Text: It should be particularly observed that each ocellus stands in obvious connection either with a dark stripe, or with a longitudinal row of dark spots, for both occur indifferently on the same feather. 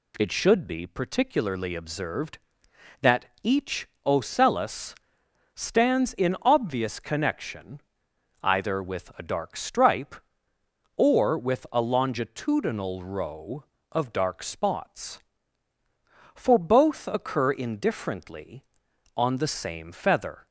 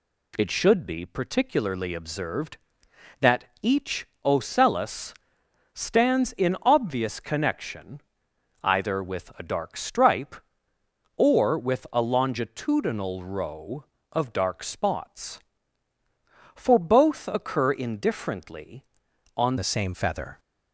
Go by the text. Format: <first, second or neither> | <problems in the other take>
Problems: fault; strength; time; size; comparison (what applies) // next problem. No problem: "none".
first | pauses between "that" and "each"; slight; at 3.4 s; 0.18 s long; slight in the first // pauses between "each" and "ocellus"; slight; at 4.0 s; 0.18 s long; slight in the first // pauses between "ocellus" and "stands"; noticeable; at 5.1 s; 0.60 s long; noticeable in the first // pauses between "connection" and "either"; noticeable; at 8.0 s; 0.62 s long; noticeable in the first // changes voice at "the"; from 19.5 s on; 0.8 s long